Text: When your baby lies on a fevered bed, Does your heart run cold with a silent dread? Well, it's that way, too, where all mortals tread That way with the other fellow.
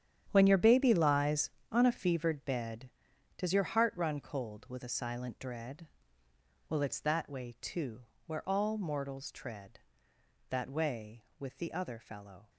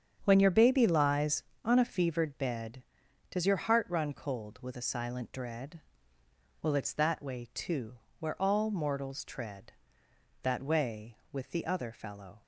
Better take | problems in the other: second | gets quieter; strong; throughout; 12.5 dB // starts louder than the rest; strong; until 1.3 s; 9.5 dB; strong in the second

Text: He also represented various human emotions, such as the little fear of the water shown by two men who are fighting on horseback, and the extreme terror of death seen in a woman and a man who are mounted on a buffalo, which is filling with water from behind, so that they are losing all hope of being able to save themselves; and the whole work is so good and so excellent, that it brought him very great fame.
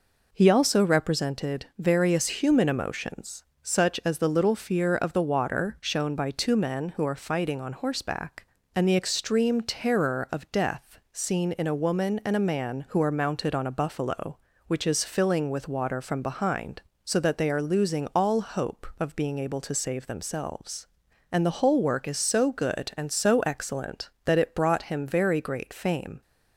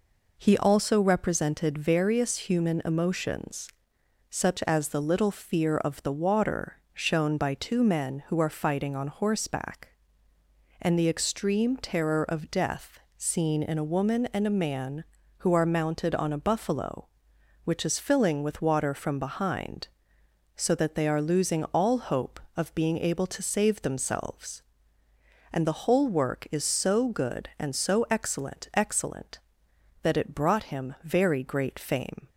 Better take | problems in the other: first | pauses between "water" and "shown"; slight; at 6.7 s; 0.16 s long // pauses between "death" and "seen"; slight; at 12.9 s; 0.18 s long // says "excellent" twice; at 28.7 s

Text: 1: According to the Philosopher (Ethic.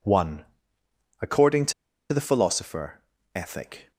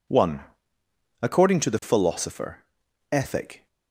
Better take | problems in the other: second | pauses between "to" and "the"; at 1.7 s; 0.39 s long

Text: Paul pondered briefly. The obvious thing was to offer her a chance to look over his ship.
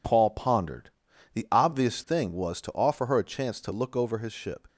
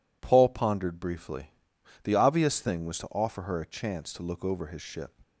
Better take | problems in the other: second | skips "briefly"; at 1.1 s

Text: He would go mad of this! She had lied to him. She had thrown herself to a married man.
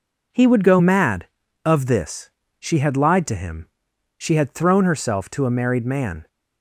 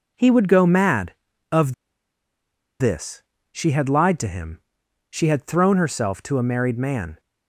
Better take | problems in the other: first | pauses between "of" and "this"; at 1.7 s; 1.0 s long

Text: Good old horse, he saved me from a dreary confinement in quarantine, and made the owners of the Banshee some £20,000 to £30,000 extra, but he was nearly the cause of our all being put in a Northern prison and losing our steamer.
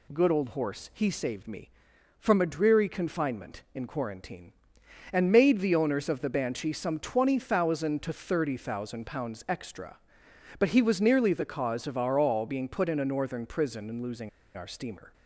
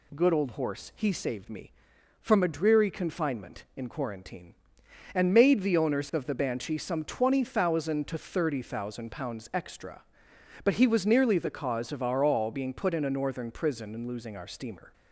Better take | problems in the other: second | pauses between "losing" and "our"; slight; at 14.2 s; 0.27 s long

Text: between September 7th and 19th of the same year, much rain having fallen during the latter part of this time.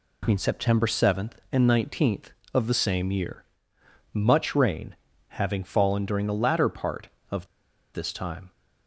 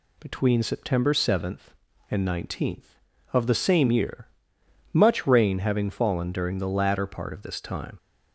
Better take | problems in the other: second | pauses between "rain" and "having"; slight; at 4.9 s; 0.32 s long // pauses between "of" and "this"; noticeable; at 7.4 s; 0.48 s long

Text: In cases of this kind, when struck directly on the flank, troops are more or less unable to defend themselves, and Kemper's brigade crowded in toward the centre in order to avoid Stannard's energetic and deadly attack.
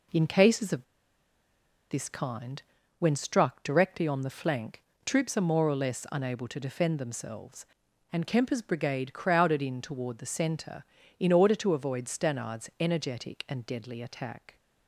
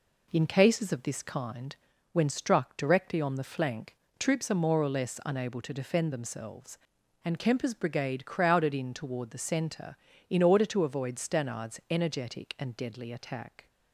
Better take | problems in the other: second | pauses between "of" and "this"; at 0.8 s; 1.0 s long

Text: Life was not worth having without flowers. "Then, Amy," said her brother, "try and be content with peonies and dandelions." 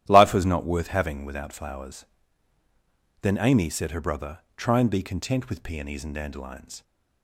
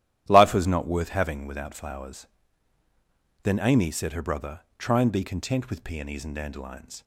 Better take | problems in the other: neither | starts louder than the rest; strong; the same in both

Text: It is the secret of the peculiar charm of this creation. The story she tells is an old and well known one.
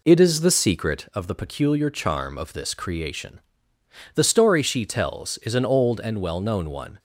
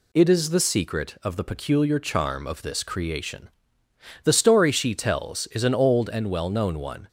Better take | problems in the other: second | starts louder than the rest; slight; until 1.1 s; 3 dB

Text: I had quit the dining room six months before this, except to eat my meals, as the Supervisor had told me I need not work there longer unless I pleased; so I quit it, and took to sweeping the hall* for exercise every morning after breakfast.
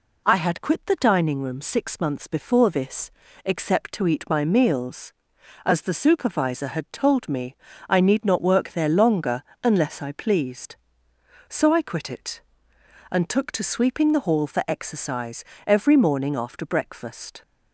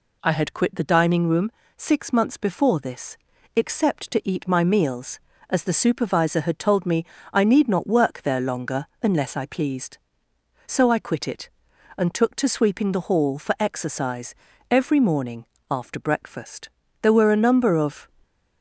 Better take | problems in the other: first | pauses between "room" and "six"; slight; at 1.4 s; 0.26 s long // pauses between "me" and "I"; slight; at 7.0 s; 0.26 s long; slight in the first // pauses between "longer" and "unless"; slight; at 8.8 s; 0.16 s long; slight in the first // pauses between "exercise" and "every"; slight; at 14.3 s; 0.36 s long; slight in the first // pauses between "morning" and "after"; slight; at 15.4 s; 0.24 s long // goes on to say "There were a number of"; noticeable; from 16.9 s on; 1.1 s long

